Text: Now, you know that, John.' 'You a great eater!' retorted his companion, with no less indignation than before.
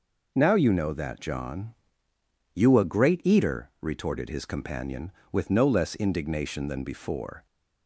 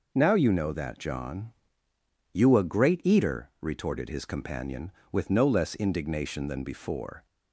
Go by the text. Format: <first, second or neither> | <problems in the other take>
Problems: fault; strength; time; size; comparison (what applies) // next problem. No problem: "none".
neither | none